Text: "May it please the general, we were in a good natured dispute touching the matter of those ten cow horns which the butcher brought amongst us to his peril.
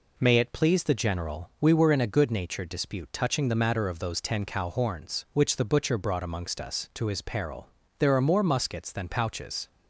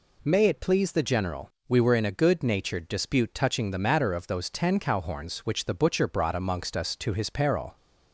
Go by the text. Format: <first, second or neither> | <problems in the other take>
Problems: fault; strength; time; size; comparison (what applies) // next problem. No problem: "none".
second | goes on to say "There are more muskets than pouches"; strong; from 7.9 s on; 1.6 s long